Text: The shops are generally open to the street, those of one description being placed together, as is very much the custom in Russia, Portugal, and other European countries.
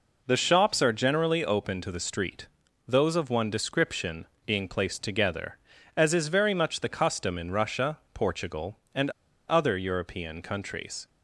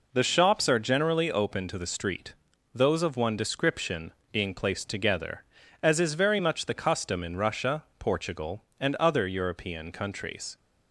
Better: second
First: pauses between "description" and "being"; slight; at 4.2 s; 0.20 s long // pauses between "and" and "other"; at 9.0 s; 0.38 s long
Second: pauses between "description" and "being"; slight; at 4.1 s; 0.20 s long

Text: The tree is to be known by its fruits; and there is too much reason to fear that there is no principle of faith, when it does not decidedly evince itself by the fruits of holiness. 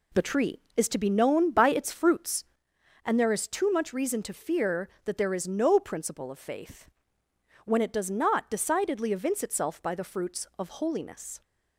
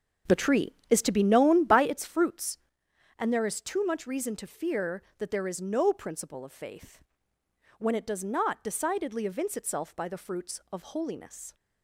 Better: first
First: none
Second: starts louder than the rest; strong; until 1.9 s; 7.5 dB

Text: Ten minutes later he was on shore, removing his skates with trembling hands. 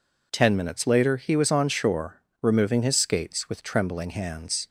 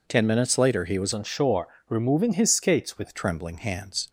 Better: first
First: none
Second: changes voice from "on" to "with"; from 1.1 to 3.1 s; 2.0 s long

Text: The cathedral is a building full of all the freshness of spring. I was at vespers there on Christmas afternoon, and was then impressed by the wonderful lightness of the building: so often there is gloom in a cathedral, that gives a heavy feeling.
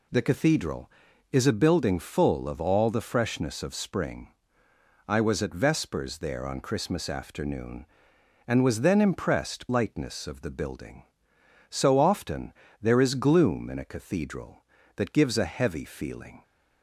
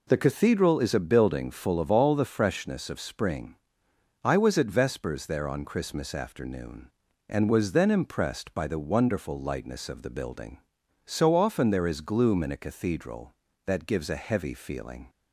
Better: second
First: skips "by the wonderful"; at 9.6 s // pauses between "often" and "there"; slight; at 12.5 s; 0.28 s long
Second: none

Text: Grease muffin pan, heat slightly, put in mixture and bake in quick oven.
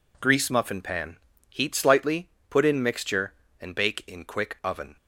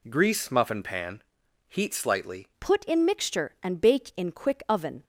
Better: first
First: none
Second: changes voice at "put"; from 2.5 s on; 2.5 s long

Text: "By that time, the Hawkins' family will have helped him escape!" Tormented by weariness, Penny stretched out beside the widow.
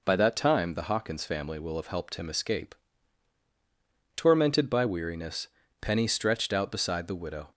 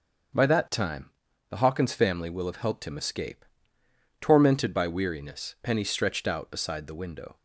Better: first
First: none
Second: starts louder than the rest; until 1.7 s; 6.5 dB // says "window" for "widow"; at 7.0 s

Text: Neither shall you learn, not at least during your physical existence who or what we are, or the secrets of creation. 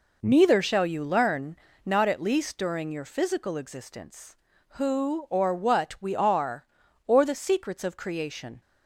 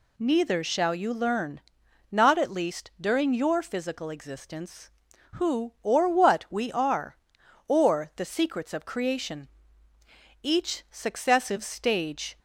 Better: first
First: none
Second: goes on to say "Each successive stage"; strong; from 10.4 s on; 1.9 s long

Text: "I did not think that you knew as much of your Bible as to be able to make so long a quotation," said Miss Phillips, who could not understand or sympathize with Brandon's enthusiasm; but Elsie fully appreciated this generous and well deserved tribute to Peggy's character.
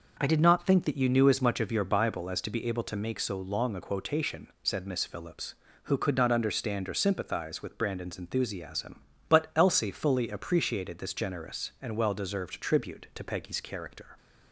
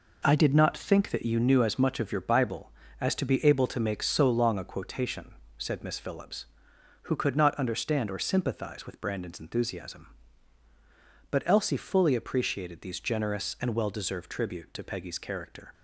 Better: first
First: none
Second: says "these" for "this"; at 12.8 s

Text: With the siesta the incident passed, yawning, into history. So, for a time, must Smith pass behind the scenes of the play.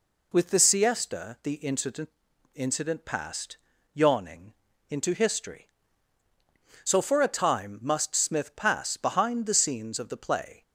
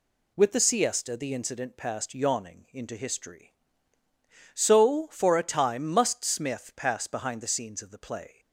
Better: second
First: says "incident" twice; at 2.5 s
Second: none

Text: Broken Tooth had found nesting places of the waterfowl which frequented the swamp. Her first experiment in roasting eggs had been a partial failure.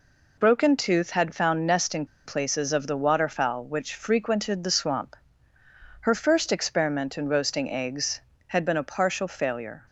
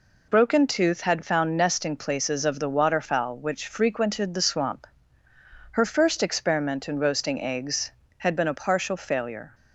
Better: second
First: pauses between "nesting" and "places"; slight; at 2.0 s; 0.20 s long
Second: none

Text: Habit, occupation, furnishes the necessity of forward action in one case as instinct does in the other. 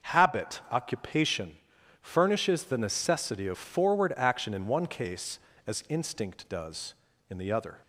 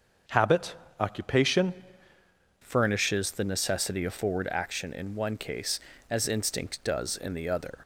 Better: first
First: none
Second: starts louder than the rest; until 1.5 s; 6.5 dB // changes voice at "furnishes"; from 2.6 s on; 5.1 s long

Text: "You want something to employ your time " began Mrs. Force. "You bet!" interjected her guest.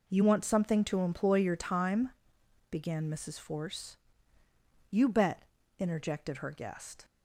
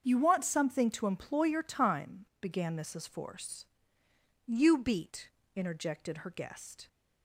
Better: first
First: none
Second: starts louder than the rest; strong; until 1.0 s; 7.5 dB // says "beat" for "bet"; at 4.7 s

